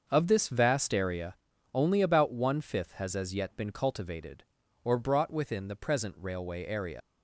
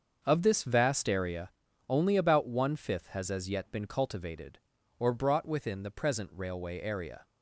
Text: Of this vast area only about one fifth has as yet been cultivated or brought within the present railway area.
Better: second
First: starts louder than the rest; until 1.0 s; 6.5 dB // pauses between "area" and "only"; at 1.3 s; 0.38 s long // leaves "area" unfinished; at 7.0 s; 90 ms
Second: starts louder than the rest; until 1.2 s; 6.5 dB // pauses between "area" and "only"; at 1.5 s; 0.38 s long

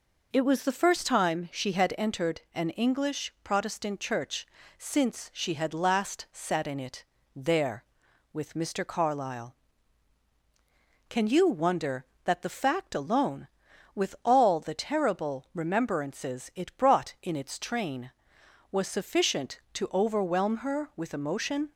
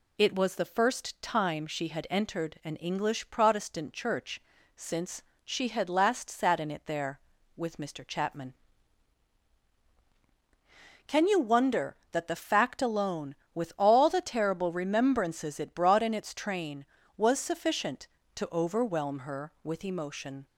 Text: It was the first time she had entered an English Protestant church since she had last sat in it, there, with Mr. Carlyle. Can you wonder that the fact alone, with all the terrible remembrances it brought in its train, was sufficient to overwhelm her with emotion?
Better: first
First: pauses between "church" and "since"; slight; at 4.4 s; 0.32 s long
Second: pauses between "church" and "since"; slight; at 4.4 s; 0.34 s long // pauses between "since" and "she"; slight; at 5.2 s; 0.20 s long // says "Chapman" for "Carlyle"; at 8.0 s

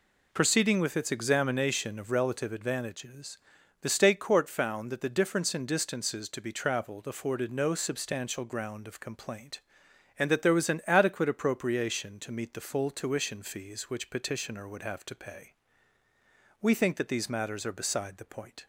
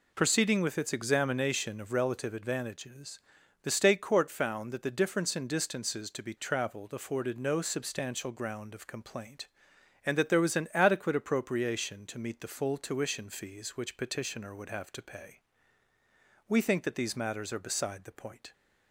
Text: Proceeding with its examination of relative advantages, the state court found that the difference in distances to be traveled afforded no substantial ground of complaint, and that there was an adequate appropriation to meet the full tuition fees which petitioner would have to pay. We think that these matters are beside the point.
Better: neither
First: none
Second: none

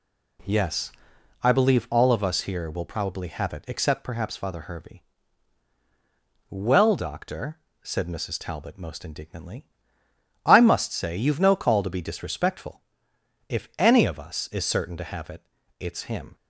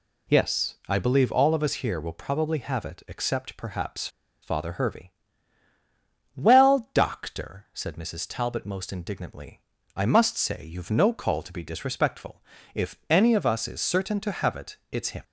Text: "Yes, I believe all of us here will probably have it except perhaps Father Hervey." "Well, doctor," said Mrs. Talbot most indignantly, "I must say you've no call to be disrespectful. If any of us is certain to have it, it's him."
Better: first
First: none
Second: pauses between "perhaps" and "Father"; slight; at 4.0 s; 0.34 s long

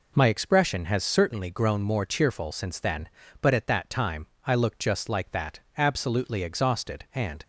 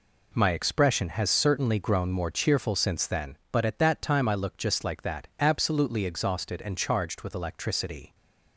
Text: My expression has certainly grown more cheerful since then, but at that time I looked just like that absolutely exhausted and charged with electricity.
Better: second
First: pauses between "time" and "I"; slight; at 4.2 s; 0.20 s long // pauses between "that" and "absolutely"; slight; at 5.5 s; 0.18 s long // stops before "charged with electricity"; at 7.4 s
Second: none

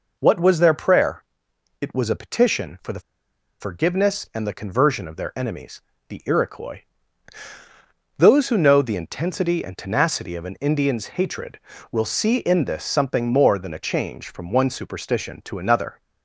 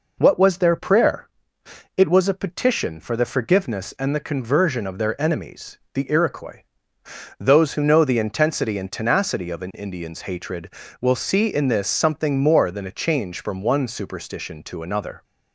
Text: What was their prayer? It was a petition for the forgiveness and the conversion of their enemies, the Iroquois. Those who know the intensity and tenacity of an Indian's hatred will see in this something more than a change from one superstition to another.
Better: second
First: pauses between "the" and "forgiveness"; noticeable; at 2.9 s; 0.60 s long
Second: none

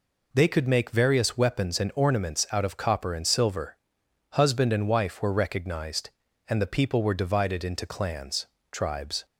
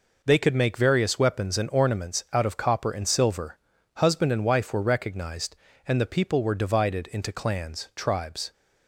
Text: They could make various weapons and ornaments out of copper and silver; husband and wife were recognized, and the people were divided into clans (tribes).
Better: neither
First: none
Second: none

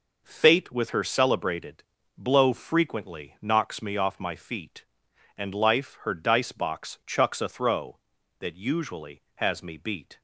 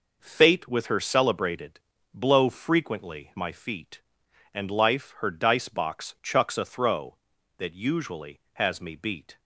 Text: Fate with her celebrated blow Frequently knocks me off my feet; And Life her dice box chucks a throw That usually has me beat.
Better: first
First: pauses between "celebrated" and "blow"; slight; at 1.8 s; 0.34 s long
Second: pauses between "celebrated" and "blow"; slight; at 1.7 s; 0.34 s long // skips "knocks me off"; at 3.3 s

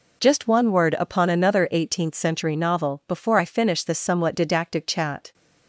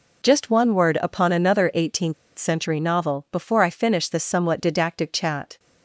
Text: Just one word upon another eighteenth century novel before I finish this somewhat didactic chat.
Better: first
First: none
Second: pauses between "eighteenth" and "century"; slight; at 2.1 s; 0.24 s long

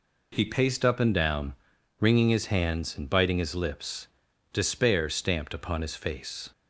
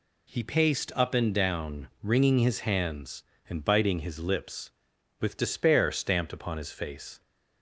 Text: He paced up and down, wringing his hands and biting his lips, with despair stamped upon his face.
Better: second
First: skips "with"; at 4.3 s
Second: none

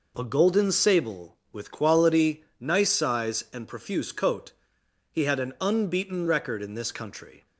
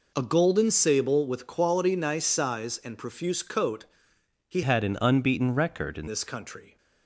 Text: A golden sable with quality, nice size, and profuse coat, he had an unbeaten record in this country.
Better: first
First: none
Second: changes voice from "had" to "in"; from 4.6 to 6.0 s; 1.4 s long

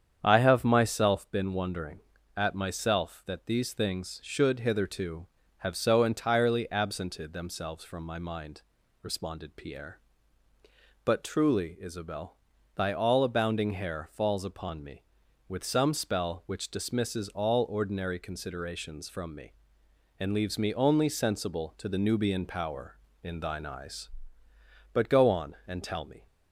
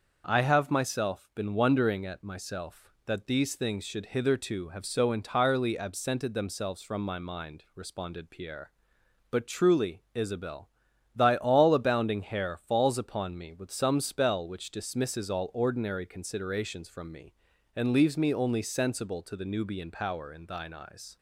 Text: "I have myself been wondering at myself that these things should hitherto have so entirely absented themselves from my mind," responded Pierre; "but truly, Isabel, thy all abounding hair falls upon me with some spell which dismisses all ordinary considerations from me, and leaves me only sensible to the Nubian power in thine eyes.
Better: second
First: starts louder than the rest; strong; until 1.2 s; 8 dB // goes on to say "But go on and tell me"; from 24.9 s on; 1.3 s long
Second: starts louder than the rest; until 1.2 s; 6 dB

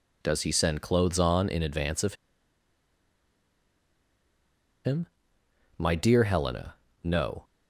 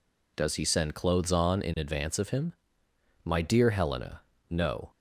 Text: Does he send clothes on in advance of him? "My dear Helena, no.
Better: second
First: pauses between "of" and "him"; strong; at 2.1 s; 2.7 s long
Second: none

